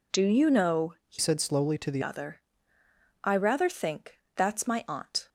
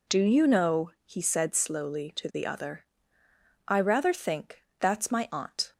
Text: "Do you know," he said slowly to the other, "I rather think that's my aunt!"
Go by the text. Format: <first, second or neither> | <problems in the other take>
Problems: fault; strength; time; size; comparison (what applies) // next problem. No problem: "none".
second | changes voice from "said" to "the"; from 1.1 to 2.0 s; 0.9 s long // pauses between "think" and "that's"; slight; at 4.2 s; 0.16 s long; slight in the second